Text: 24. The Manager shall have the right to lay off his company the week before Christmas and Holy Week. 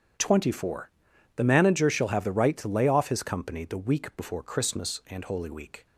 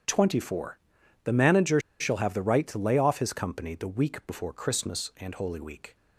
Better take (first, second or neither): first